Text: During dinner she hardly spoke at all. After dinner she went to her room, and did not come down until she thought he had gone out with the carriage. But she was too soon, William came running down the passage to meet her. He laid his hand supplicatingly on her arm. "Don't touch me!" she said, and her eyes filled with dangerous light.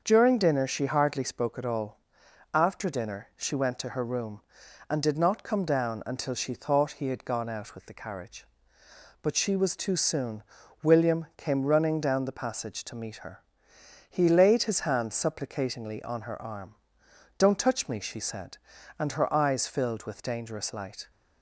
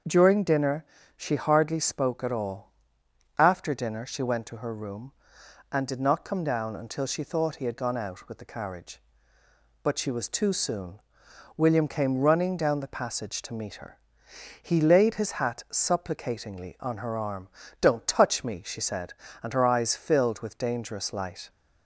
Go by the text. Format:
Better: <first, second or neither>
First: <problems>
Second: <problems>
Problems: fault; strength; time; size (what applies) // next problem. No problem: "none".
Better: first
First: starts louder than the rest; until 1.0 s; 6.5 dB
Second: starts louder than the rest; until 1.3 s; 6.5 dB // pauses between "dinner" and "she"; slight; at 0.8 s; 0.32 s long // says "hat" for "hand"; at 15.3 s